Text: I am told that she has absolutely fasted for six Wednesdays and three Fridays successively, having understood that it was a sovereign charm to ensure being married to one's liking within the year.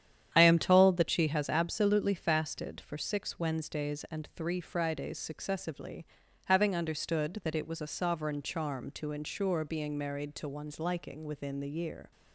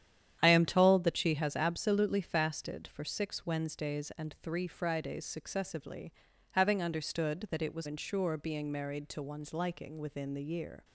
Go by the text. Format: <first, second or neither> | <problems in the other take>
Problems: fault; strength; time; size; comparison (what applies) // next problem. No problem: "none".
first | starts louder than the rest; strong; until 1.4 s; 9.5 dB; strong in the first // skips "a sovereign charm to"; at 7.8 s